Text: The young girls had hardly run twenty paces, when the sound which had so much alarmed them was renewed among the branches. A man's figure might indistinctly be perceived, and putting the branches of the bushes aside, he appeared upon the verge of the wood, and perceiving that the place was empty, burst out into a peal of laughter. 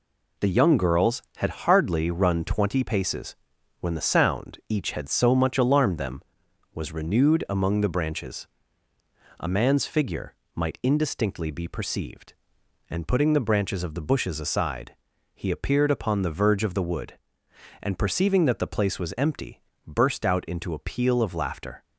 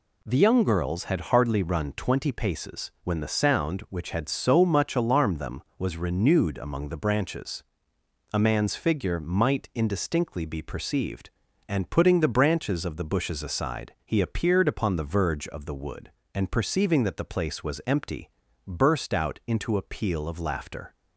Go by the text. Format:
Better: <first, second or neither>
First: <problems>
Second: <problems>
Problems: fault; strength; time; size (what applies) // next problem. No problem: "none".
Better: second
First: says "each" for "which"; at 4.6 s // pauses between "figure" and "might"; slight; at 10.3 s; 0.20 s long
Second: none